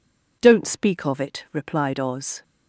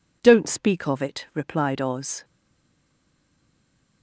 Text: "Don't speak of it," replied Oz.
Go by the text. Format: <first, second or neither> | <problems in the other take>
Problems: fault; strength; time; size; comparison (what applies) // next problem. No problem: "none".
first | stays silent after the last word; noticeable; from 2.2 s on; 1.8 s long